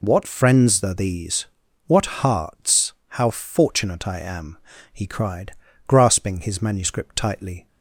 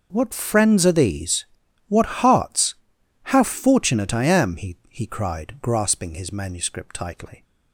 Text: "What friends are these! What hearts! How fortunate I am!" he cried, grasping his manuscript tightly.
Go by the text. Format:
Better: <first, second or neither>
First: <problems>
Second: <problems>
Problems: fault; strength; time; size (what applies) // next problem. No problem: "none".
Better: first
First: none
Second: says "he" twice; at 4.8 s